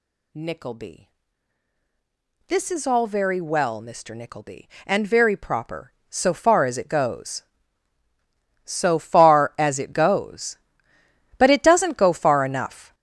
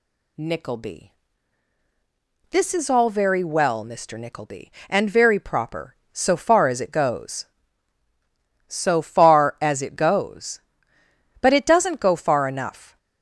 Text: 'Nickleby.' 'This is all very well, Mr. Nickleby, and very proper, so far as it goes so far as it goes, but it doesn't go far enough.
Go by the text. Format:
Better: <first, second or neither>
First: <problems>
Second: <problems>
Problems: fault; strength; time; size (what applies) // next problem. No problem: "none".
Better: second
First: gets louder; strong; throughout; 9.5 dB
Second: none